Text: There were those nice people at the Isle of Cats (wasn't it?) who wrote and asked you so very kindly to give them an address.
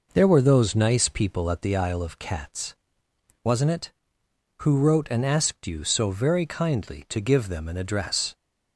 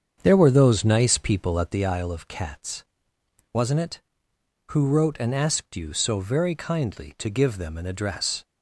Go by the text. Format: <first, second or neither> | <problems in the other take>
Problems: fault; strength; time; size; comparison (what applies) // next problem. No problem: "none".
first | starts louder than the rest; strong; until 2.0 s; 7.5 dB